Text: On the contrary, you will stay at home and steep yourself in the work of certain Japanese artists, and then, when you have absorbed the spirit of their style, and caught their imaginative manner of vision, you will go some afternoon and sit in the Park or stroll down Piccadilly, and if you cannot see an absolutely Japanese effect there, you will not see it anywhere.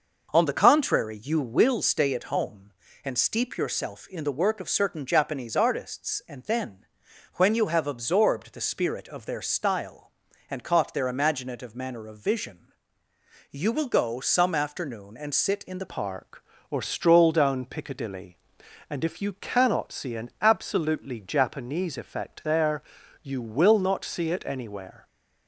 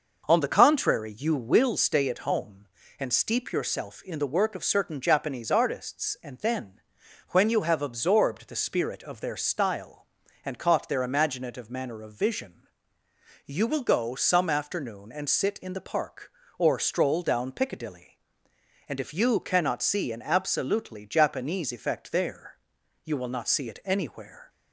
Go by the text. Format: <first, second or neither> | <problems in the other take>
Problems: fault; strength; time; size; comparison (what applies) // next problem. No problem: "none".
second | changes voice at "Park"; from 15.8 s on; 9.2 s long